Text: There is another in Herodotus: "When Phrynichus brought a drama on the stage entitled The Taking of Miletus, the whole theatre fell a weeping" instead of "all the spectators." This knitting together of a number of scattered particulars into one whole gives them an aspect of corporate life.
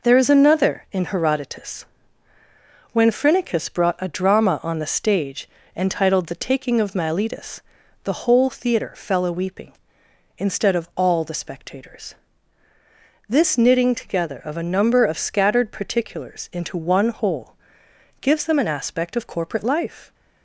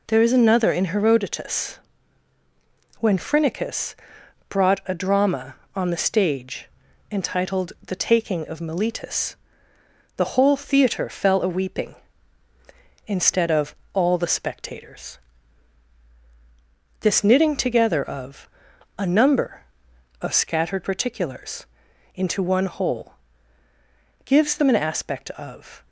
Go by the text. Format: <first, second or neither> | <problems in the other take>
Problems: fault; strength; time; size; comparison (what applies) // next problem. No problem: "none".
first | pauses between "Phrynichus" and "brought"; noticeable; at 3.9 s; 0.54 s long // pauses between "stage" and "entitled"; at 6.6 s; 0.42 s long; slight in the first // pauses between "of" and "all"; slight; at 13.7 s; 0.20 s long // pauses between "of" and "a"; noticeable; at 18.4 s; 0.48 s long // pauses between "particulars" and "into"; noticeable; at 21.6 s; 0.48 s long // pauses between "whole" and "gives"; at 23.1 s; 1.1 s long; noticeable in the first // stops before "corporate life"; at 25.8 s